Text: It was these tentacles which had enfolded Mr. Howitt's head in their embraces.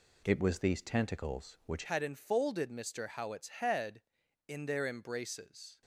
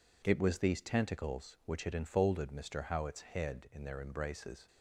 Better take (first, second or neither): second